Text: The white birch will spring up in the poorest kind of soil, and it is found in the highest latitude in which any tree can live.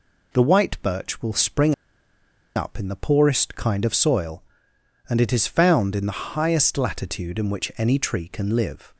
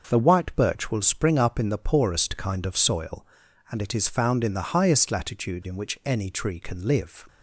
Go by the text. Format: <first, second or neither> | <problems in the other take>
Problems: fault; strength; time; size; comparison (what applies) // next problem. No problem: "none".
second | pauses between "spring" and "up"; noticeable; at 1.7 s; 0.82 s long